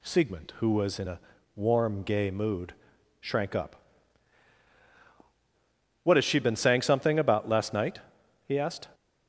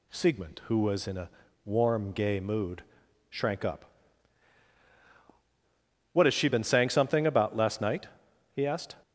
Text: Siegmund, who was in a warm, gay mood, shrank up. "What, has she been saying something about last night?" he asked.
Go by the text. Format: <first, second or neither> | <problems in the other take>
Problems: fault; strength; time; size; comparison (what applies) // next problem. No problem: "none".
neither | pauses between "a" and "warm"; slight; the same in both